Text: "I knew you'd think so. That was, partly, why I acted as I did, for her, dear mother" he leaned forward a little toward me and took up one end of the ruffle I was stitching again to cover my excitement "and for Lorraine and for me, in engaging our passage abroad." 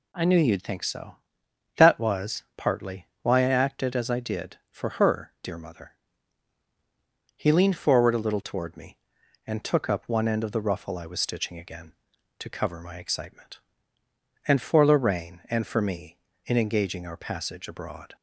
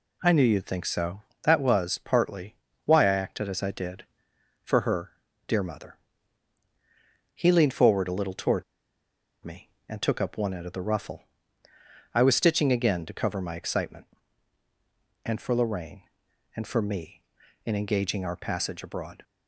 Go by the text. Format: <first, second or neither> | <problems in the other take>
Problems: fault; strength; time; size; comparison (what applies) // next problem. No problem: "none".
first | pauses between "mother" and "he"; strong; at 5.9 s; 1.4 s long; strong in the first // pauses between "toward" and "me"; noticeable; at 8.6 s; 0.81 s long // pauses between "ruffle" and "I"; noticeable; at 11.2 s; 0.90 s long